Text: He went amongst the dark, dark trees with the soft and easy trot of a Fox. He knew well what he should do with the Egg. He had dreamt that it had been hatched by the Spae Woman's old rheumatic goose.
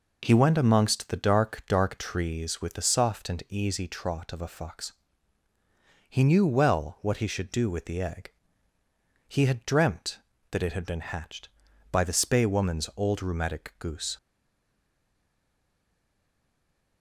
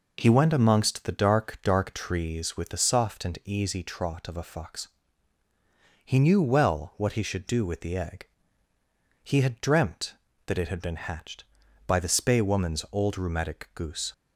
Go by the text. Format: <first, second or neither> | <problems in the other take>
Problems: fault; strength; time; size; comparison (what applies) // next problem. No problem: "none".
second | stays silent after the last word; strong; from 14.1 s on; 2.9 s long